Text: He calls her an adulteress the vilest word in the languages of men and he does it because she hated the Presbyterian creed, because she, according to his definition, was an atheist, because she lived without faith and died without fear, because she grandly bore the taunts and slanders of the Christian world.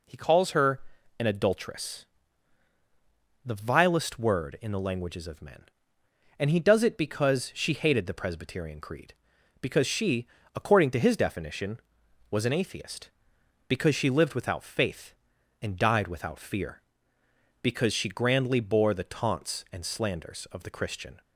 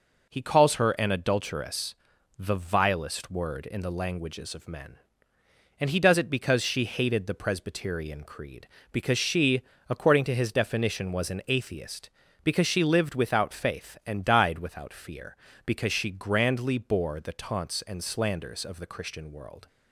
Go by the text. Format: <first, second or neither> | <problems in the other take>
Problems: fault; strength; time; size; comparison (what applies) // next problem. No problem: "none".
second | pauses between "her" and "an"; at 0.7 s; 0.40 s long // pauses between "adulteress" and "the"; strong; at 2.0 s; 1.4 s long; also in the second // stops before "world"; at 21.2 s